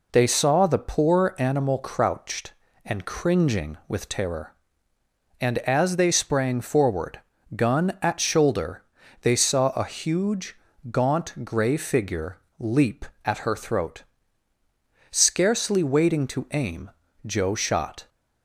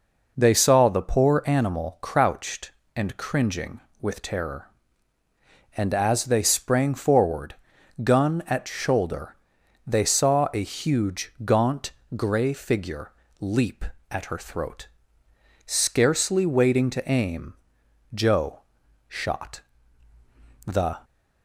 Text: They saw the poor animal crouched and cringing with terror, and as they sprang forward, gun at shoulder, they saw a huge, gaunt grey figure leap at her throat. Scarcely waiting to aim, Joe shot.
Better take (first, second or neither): first